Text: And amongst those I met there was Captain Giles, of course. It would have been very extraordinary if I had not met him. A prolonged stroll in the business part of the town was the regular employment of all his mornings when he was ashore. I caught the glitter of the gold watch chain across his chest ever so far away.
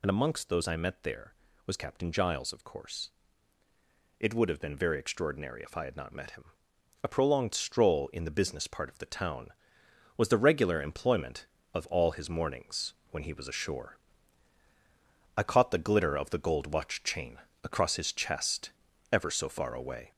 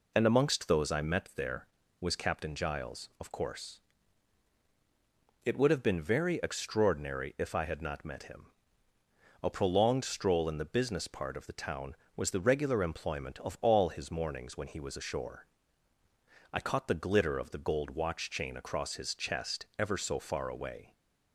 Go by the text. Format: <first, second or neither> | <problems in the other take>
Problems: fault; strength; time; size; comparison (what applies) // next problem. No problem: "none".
second | gets louder; noticeable; throughout; 4 dB // pauses between "mornings" and "when"; slight; at 12.9 s; 0.18 s long // pauses between "chain" and "across"; slight; at 17.3 s; 0.26 s long // pauses between "chest" and "ever"; at 18.7 s; 0.40 s long